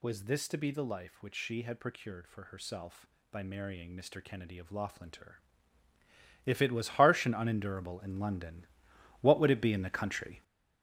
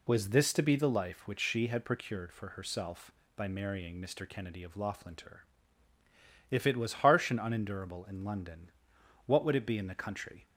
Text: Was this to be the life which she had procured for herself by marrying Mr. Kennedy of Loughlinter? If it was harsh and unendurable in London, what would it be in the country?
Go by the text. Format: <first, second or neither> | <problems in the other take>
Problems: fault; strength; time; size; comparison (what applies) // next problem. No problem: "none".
second | gets louder; strong; throughout; 7.5 dB